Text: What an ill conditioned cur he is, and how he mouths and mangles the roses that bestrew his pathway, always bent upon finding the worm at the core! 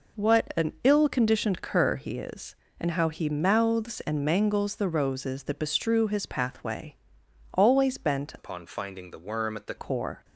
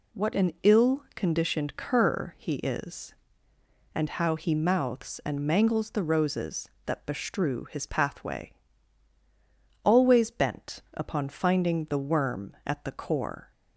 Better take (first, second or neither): second